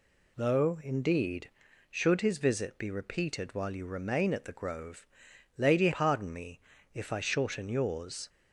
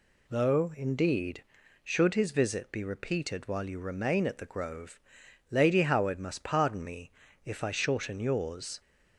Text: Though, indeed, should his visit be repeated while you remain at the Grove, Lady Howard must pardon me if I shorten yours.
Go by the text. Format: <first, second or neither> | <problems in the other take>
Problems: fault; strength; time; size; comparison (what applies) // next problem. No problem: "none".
second | skips "Howard must"; at 5.9 s // pauses between "me" and "if"; slight; at 6.5 s; 0.34 s long; slight in the second